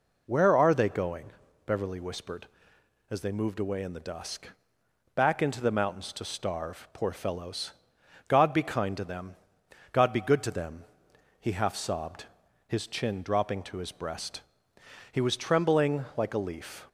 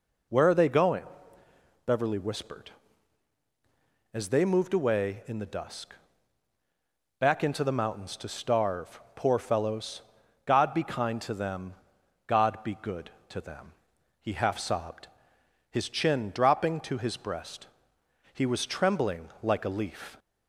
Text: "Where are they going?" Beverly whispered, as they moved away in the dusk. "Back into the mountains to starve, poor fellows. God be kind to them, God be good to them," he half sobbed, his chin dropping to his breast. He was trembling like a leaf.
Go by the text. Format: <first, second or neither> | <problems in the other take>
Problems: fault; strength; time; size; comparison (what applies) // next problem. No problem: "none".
neither | none